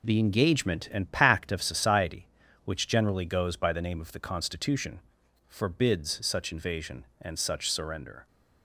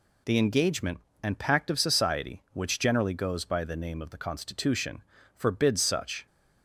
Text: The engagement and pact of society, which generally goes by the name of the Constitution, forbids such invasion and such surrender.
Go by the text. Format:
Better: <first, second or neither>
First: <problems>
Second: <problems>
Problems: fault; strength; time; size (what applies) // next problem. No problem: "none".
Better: first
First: none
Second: stops before "invasion and such surrender"; at 6.2 s